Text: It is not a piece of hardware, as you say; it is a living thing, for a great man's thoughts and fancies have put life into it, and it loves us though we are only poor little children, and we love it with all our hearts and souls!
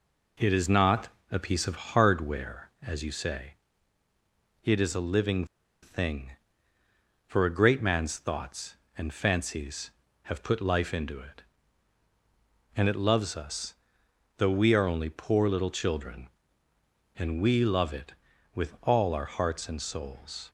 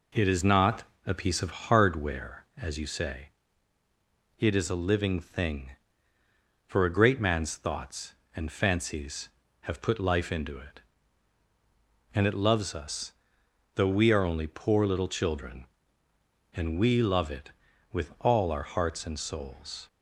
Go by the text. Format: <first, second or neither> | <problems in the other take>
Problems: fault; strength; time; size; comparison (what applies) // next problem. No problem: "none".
second | pauses between "not" and "a"; slight; at 1.0 s; 0.24 s long; slight in the second // pauses between "living" and "thing"; at 5.4 s; 0.38 s long // pauses between "us" and "though"; noticeable; at 13.7 s; 0.62 s long; noticeable in the second